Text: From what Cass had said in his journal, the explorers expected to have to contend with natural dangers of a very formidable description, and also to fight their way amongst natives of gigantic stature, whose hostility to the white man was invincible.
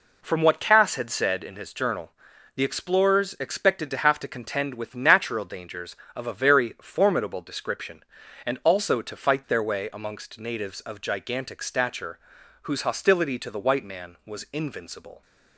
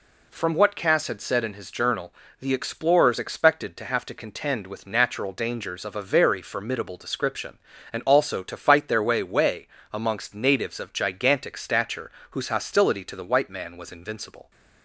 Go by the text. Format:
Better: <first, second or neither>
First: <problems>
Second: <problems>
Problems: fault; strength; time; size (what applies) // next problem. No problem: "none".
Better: first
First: none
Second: says "way" twice; at 9.2 s